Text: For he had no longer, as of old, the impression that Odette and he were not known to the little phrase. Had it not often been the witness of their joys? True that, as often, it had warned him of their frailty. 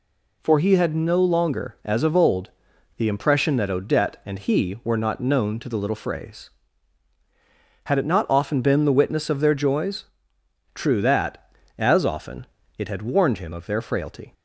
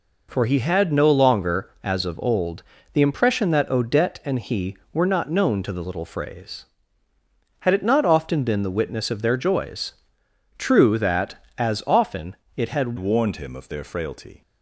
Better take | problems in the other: first | changes voice at "warned"; from 12.9 s on; 1.5 s long

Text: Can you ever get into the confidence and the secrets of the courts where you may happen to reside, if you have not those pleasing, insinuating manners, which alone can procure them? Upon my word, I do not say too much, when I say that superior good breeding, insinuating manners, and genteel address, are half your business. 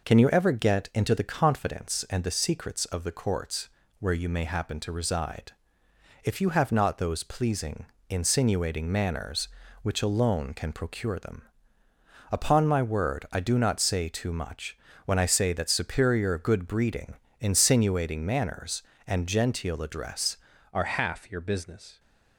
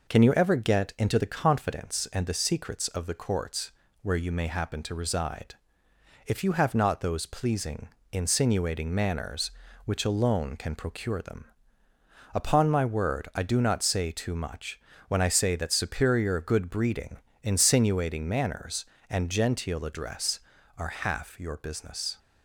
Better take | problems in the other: second | pauses between "courts" and "where"; slight; at 3.6 s; 0.32 s long; slight in the second // changes voice at "are"; from 20.7 s on; 1.2 s long

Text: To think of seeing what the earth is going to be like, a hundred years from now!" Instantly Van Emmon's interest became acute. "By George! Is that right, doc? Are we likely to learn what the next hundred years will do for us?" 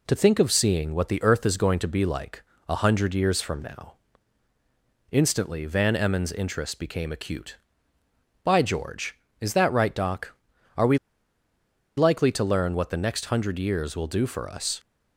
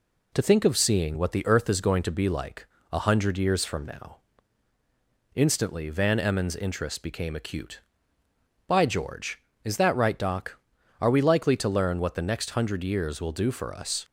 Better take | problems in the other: second | pauses between "we" and "likely"; at 10.9 s; 0.99 s long

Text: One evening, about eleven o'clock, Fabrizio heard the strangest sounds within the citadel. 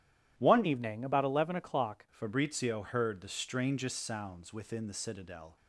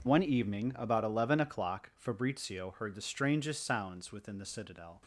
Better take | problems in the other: second | starts louder than the rest; strong; until 1.3 s; 12 dB // changes voice from "evening" to "o'clock"; from 0.6 to 2.0 s; 1.4 s long

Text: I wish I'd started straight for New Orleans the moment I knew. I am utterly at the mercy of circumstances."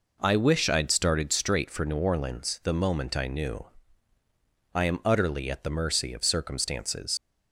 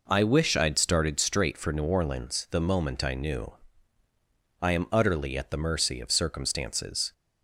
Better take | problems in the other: second | leaves "circumstances" unfinished; at 7.1 s; 80 ms

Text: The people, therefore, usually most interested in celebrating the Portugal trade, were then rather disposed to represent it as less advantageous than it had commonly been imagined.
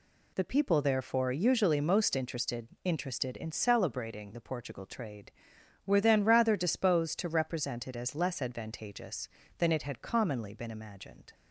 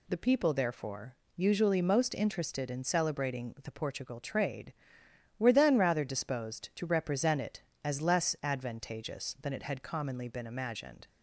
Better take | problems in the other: second | says "interested" twice; at 2.8 s

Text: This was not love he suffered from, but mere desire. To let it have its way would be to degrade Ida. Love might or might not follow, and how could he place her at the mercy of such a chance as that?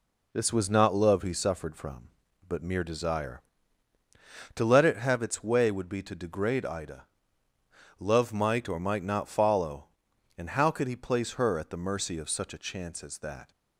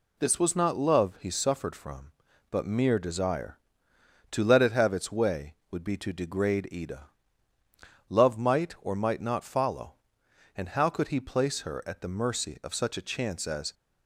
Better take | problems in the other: first | stops before "that"; at 13.7 s

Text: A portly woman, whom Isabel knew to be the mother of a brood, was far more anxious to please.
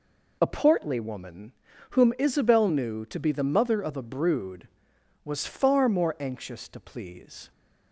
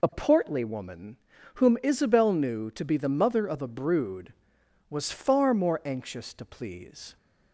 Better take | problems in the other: neither | none

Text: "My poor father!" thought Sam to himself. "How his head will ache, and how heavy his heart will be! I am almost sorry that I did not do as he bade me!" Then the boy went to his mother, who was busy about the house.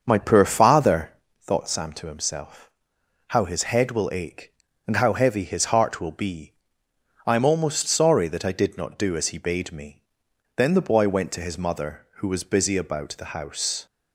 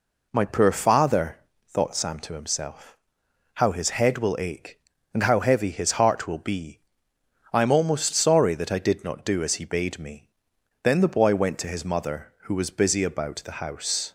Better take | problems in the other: second | starts louder than the rest; until 1.3 s; 6.5 dB

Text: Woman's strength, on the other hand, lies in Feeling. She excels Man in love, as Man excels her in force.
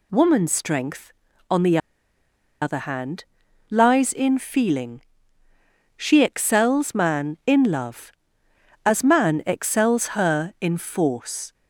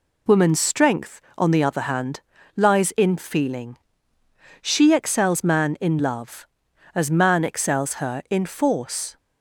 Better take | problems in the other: second | pauses between "the" and "other"; noticeable; at 1.7 s; 0.84 s long

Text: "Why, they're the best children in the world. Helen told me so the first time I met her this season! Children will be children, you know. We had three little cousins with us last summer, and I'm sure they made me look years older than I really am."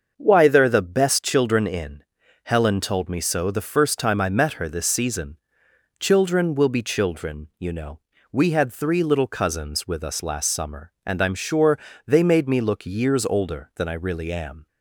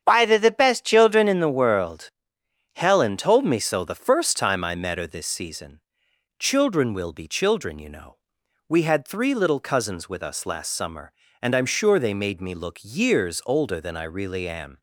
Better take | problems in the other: second | starts louder than the rest; until 1.1 s; 6.5 dB; strong in the second // skips "the world"; at 2.2 s // pauses between "sure" and "they"; slight; at 11.7 s; 0.28 s long

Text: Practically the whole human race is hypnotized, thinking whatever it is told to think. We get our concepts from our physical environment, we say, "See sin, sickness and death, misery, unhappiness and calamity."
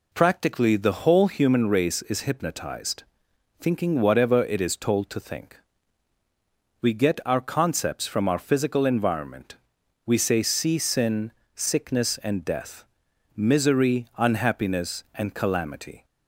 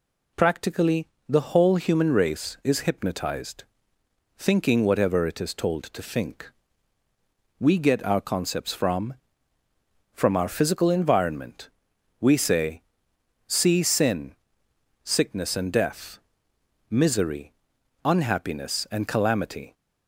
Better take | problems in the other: first | pauses between "Practically" and "the"; slight; at 1.0 s; 0.20 s long // says "from" twice; at 10.1 s

